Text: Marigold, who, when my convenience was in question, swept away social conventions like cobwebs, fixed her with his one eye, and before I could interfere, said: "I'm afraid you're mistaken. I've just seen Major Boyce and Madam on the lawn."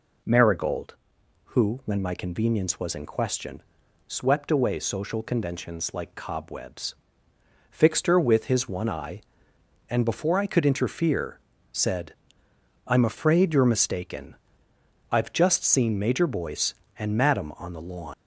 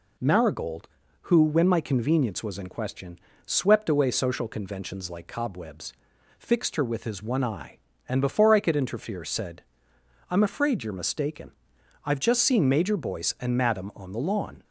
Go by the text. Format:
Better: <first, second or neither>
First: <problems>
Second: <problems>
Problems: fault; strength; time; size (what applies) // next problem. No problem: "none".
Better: second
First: leaves "lawn" unfinished; at 18.1 s; 115 ms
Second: none